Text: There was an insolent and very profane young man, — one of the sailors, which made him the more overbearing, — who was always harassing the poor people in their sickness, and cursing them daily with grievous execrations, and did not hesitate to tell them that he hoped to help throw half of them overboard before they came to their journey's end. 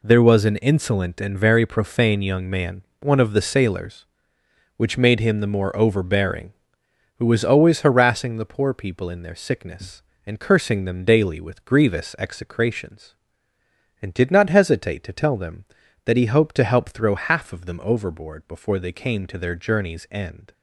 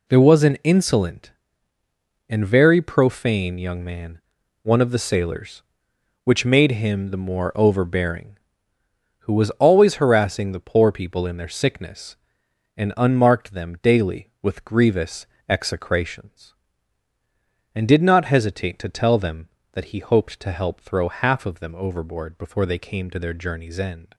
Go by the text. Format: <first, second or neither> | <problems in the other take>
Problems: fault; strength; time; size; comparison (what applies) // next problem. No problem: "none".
first | says "unmarked" for "cursing"; at 12.9 s // pauses between "grievous" and "execrations"; slight; at 15.2 s; 0.22 s long